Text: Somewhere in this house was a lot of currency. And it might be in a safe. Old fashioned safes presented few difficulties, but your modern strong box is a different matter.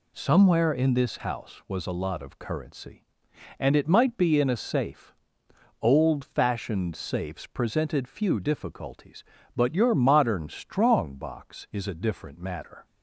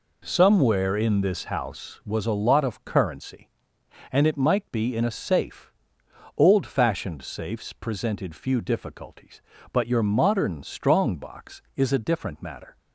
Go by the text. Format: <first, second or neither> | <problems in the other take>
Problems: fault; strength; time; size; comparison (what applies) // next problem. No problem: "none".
neither | none